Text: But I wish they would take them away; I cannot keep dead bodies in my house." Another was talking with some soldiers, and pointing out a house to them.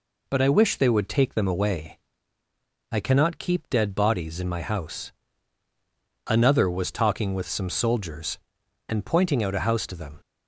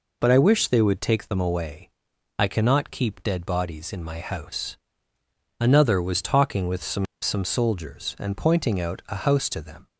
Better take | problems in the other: first | says "some" twice; at 7.2 s

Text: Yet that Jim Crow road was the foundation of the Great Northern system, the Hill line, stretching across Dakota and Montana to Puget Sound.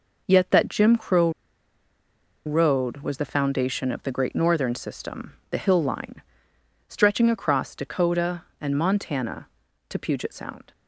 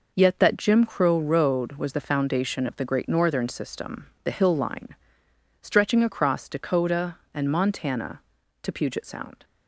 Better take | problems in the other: second | pauses between "Crow" and "road"; at 1.3 s; 1.1 s long

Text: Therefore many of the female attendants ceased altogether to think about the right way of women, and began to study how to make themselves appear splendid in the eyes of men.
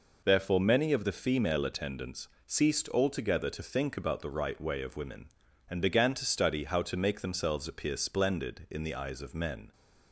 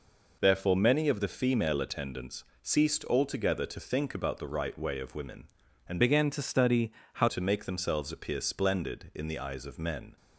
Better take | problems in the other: first | pauses between "attendants" and "ceased"; slight; at 2.4 s; 0.18 s long; slight in the first // changes voice from "began" to "how"; from 6.0 to 7.2 s; 1.2 s long // pauses between "study" and "how"; slight; at 6.9 s; 0.24 s long

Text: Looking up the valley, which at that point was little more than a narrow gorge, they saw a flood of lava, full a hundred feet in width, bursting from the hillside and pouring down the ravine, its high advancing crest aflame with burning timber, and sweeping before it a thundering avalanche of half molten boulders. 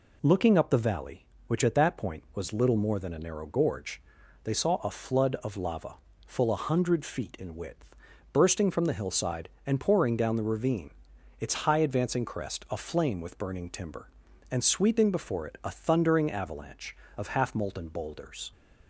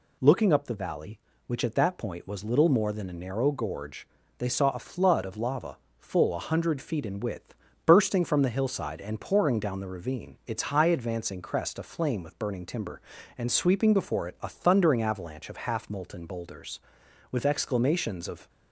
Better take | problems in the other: first | goes on to say "With exclamations of"; noticeable; from 17.3 s on; 1.1 s long

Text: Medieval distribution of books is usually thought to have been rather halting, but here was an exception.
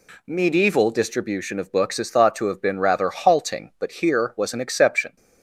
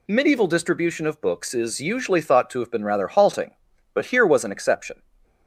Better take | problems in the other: second | skips "usually"; at 2.0 s

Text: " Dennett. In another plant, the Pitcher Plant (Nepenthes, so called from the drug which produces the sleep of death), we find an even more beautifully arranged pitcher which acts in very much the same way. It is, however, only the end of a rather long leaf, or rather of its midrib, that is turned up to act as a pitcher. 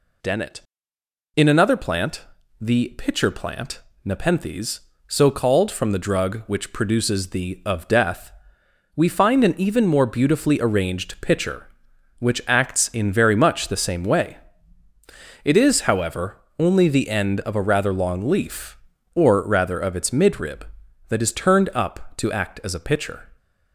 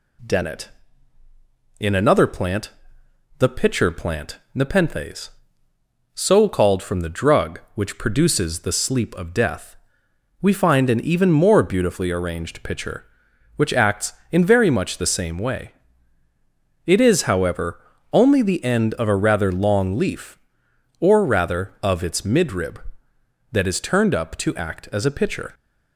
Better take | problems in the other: second | skips "sleep"; at 7.6 s

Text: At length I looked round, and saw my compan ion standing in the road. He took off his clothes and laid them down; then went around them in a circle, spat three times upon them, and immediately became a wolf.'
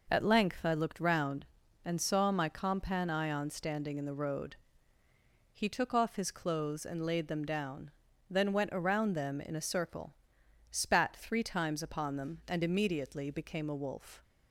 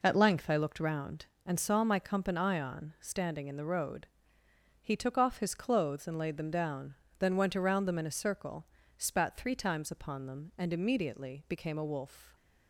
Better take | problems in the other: neither | none

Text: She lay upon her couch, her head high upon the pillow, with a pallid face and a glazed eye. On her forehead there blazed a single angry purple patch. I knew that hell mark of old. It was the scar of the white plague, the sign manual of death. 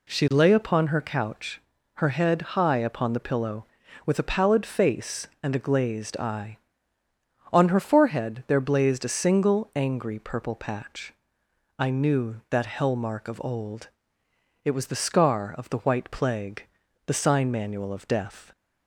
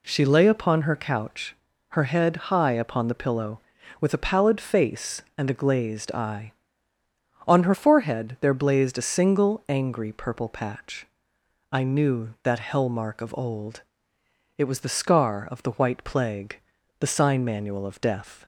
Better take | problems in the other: neither | pauses between "head" and "high"; slight; the same in both

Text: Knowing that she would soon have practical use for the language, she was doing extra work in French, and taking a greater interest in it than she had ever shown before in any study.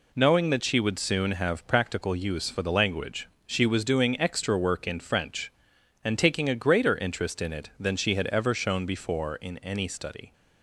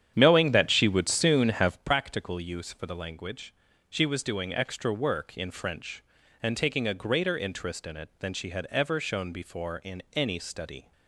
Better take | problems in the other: first | starts louder than the rest; strong; until 1.8 s; 9.5 dB

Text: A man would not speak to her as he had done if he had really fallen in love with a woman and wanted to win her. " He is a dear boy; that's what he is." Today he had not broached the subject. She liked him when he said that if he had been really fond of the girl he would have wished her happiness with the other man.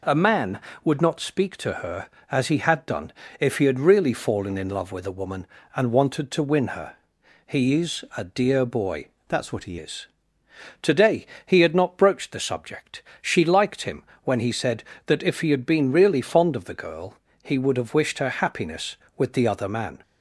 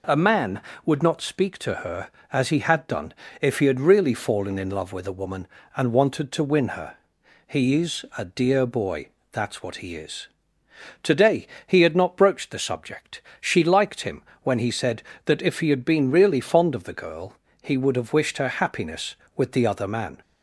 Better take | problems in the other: second | pauses between "done" and "if"; slight; at 3.1 s; 0.28 s long; slight in the second // changes voice from "that's" to "he"; from 9.2 to 9.7 s; 0.5 s long // pauses between "Today" and "he"; slight; at 11.2 s; 0.20 s long; slight in the second // pauses between "him" and "when"; slight; at 14.0 s; 0.20 s long; slight in the second // pauses between "girl" and "he"; slight; at 17.1 s; 0.26 s long; slight in the second

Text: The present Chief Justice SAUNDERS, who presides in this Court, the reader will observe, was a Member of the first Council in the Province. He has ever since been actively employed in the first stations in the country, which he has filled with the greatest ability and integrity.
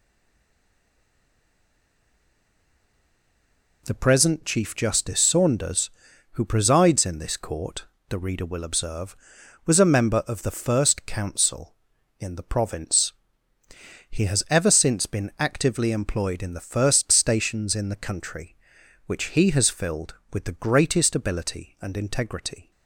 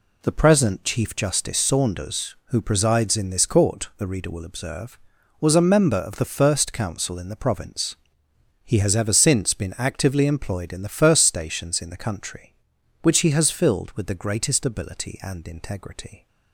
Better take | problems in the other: second | stays silent before the first word; strong; until 3.8 s; 3.8 s long

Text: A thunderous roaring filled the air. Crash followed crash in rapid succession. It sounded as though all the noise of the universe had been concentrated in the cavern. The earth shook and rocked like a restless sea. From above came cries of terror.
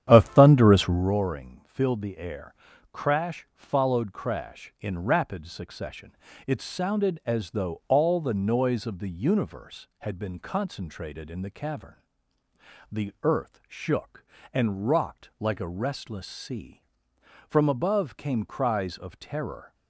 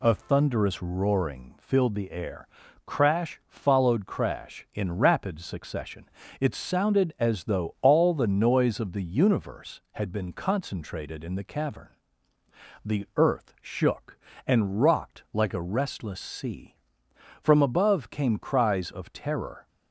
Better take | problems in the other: second | starts louder than the rest; strong; until 1.2 s; 10 dB

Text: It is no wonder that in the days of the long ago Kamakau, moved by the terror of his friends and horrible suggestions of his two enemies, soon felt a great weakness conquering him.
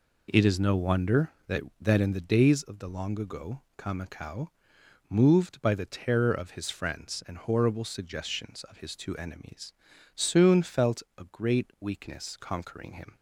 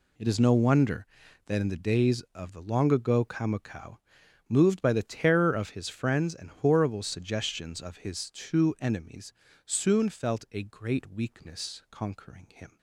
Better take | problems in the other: second | says "that" twice; at 1.8 s // pauses between "ago" and "Kamakau"; slight; at 3.6 s; 0.18 s long // pauses between "felt" and "a"; slight; at 11.0 s; 0.16 s long

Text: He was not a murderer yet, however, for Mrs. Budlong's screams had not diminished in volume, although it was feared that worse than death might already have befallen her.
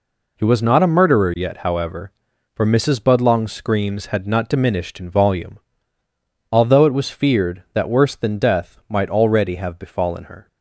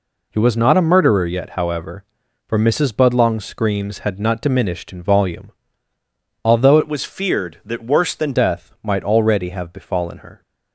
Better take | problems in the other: first | changes voice from "it" to "than"; from 6.8 to 8.3 s; 1.5 s long

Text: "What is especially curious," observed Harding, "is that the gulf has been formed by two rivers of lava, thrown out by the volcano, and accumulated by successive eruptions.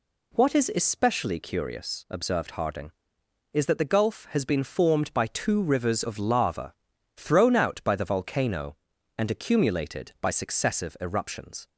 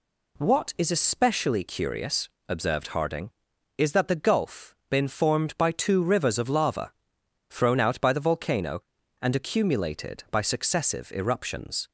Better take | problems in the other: first | skips "has"; at 4.8 s

